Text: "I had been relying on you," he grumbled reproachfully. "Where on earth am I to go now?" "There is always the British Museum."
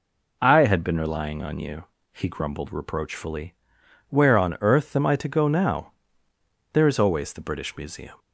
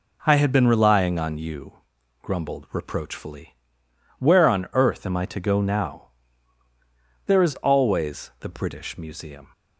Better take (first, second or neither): first